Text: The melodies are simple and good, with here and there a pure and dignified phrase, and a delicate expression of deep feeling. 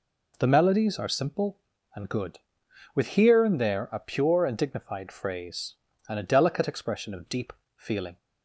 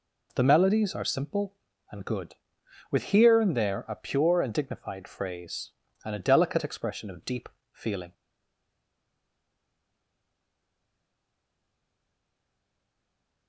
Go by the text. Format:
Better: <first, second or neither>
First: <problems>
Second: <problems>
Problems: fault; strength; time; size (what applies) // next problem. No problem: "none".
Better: first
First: pauses between "deep" and "feeling"; slight; at 7.5 s; 0.24 s long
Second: pauses between "deep" and "feeling"; slight; at 7.4 s; 0.24 s long // stays silent after the last word; strong; from 8.1 s on; 5.3 s long